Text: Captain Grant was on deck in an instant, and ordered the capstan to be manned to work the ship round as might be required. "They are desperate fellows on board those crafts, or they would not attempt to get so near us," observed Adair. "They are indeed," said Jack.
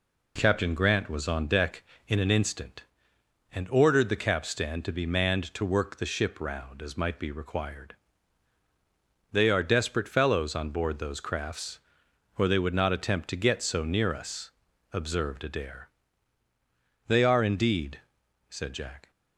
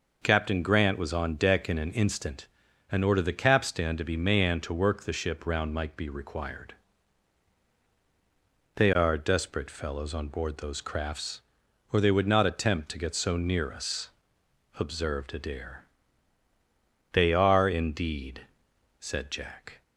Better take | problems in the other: first | skips "as"; at 5.7 s

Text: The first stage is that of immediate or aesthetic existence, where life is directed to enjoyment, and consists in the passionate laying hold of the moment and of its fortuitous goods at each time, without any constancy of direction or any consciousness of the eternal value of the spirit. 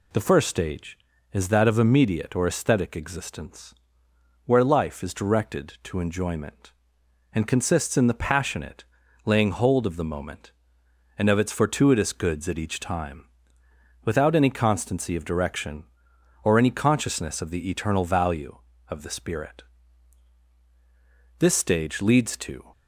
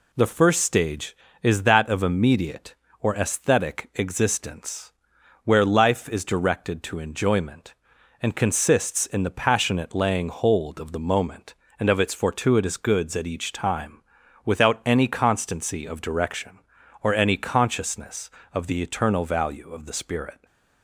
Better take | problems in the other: second | pauses between "passionate" and "laying"; at 8.8 s; 0.40 s long // goes on to say "This stage leads to"; from 21.3 s on; 1.3 s long

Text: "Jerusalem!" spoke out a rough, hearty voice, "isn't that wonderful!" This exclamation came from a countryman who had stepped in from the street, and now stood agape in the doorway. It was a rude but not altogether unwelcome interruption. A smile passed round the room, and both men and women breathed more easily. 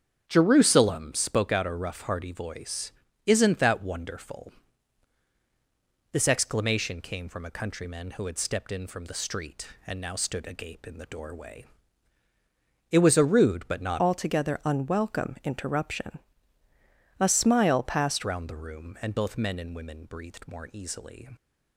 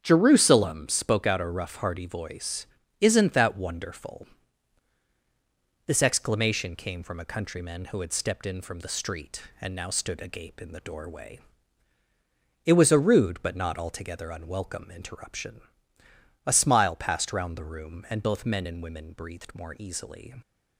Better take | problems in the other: second | starts louder than the rest; strong; until 1.2 s; 8 dB; strong in the second // changes voice from "altogether" to "passed"; from 13.9 to 18.2 s; 4.3 s long

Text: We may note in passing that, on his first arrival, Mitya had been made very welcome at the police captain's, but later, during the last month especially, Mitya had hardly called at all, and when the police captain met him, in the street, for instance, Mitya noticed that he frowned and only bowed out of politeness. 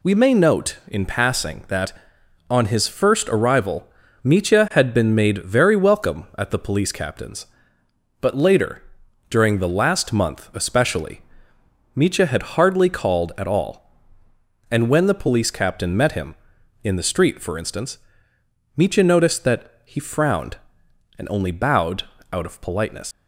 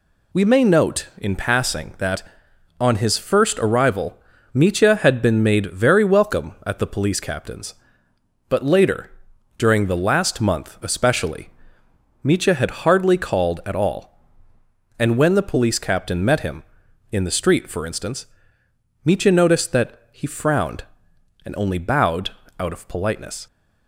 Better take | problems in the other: second | pauses between "bowed" and "out"; slight; at 22.0 s; 0.28 s long; slight in the second // leaves "politeness" unfinished; at 23.1 s; 85 ms

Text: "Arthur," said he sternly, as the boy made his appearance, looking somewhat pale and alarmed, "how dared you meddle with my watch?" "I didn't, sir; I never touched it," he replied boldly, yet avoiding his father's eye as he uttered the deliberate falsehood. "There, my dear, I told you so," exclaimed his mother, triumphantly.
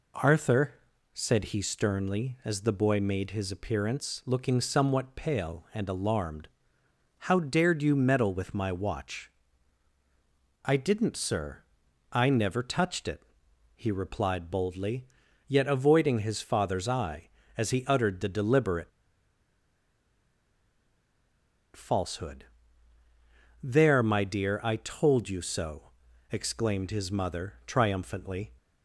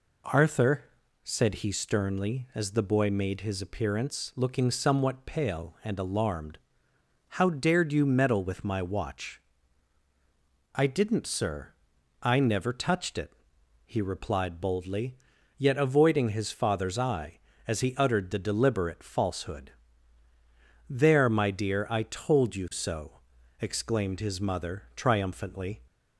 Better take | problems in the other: second | pauses between "deliberate" and "falsehood"; strong; at 18.9 s; 2.8 s long

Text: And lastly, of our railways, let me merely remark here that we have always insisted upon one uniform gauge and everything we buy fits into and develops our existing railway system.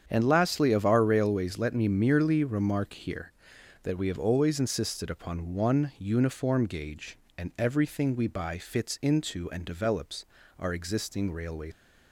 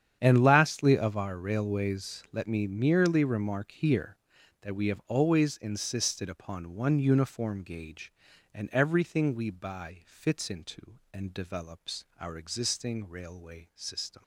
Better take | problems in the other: second | starts louder than the rest; strong; until 1.0 s; 8 dB; strong in the second // pauses between "develops" and "our"; slight; at 10.2 s; 0.34 s long // stops before "system"; at 11.7 s

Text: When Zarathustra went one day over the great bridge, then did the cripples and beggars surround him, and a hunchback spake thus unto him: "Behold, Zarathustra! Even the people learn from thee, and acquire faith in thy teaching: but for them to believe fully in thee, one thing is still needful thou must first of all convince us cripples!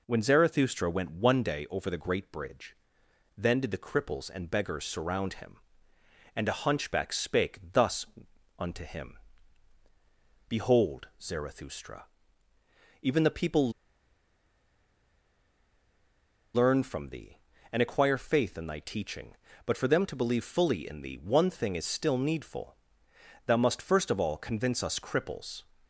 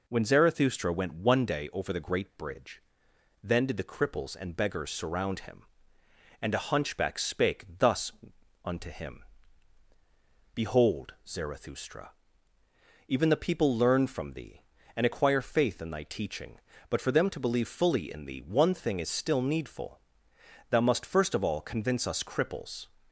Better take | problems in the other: second | pauses between "spake" and "thus"; slight; at 7.5 s; 0.16 s long; slight in the second // pauses between "thus" and "unto"; noticeable; at 8.0 s; 0.52 s long; noticeable in the second // pauses between "people" and "learn"; strong; at 13.6 s; 2.8 s long // pauses between "needful" and "thou"; noticeable; at 22.7 s; 0.70 s long; noticeable in the second

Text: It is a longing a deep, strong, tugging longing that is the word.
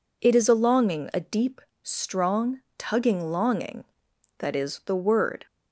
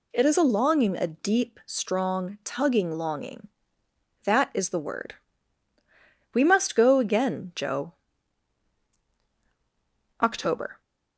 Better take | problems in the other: first | goes on to say "We must go again Joe October"; strong; from 6.3 s on; 4.4 s long

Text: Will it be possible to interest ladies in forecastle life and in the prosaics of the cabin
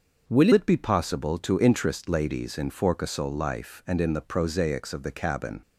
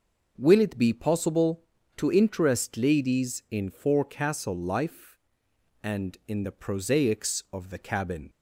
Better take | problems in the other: second | starts louder than the rest; until 1.3 s; 6 dB // changes voice at "it"; from 0.5 s on; 5.1 s long

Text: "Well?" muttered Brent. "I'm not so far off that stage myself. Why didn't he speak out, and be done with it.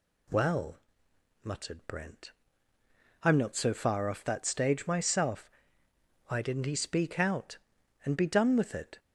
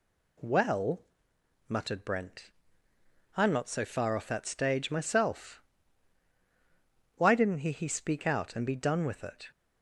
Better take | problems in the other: first | says "he" twice; at 7.7 s

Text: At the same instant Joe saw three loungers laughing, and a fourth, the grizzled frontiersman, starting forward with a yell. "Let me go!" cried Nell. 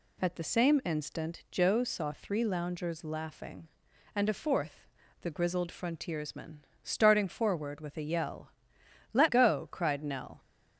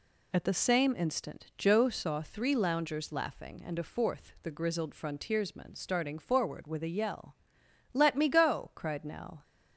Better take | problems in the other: second | skips "me"; at 9.2 s

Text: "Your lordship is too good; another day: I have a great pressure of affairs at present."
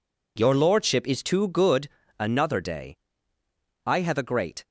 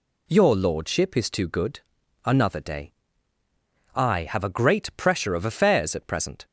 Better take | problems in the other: second | stops before "pressure of affairs at present"; at 4.6 s

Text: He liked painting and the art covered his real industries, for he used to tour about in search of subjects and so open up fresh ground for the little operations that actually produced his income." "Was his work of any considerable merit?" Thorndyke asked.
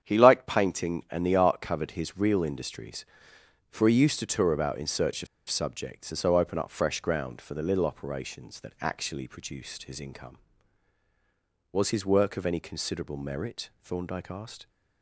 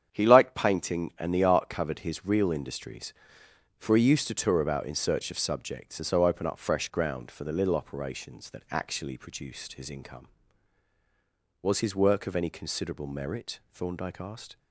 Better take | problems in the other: second | starts louder than the rest; strong; until 1.0 s; 8.5 dB; strong in the second // pauses between "of" and "subjects"; slight; at 5.2 s; 0.23 s long

